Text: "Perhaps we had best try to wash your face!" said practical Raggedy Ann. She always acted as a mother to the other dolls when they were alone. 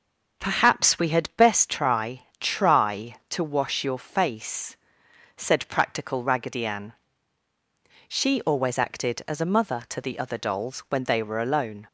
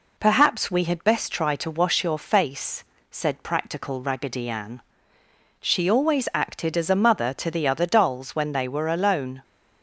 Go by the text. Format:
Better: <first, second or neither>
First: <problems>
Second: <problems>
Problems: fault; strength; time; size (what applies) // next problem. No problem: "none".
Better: second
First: starts louder than the rest; until 1.4 s; 6.5 dB // says "try" twice; at 2.4 s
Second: none